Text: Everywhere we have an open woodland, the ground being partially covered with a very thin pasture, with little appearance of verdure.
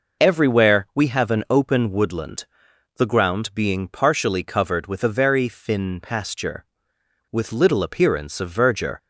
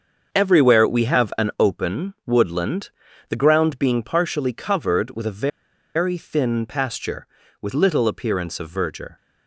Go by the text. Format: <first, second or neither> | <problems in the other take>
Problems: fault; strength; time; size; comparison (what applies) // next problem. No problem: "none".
first | starts louder than the rest; until 1.3 s; 6.5 dB // pauses between "a" and "very"; noticeable; at 5.4 s; 0.46 s long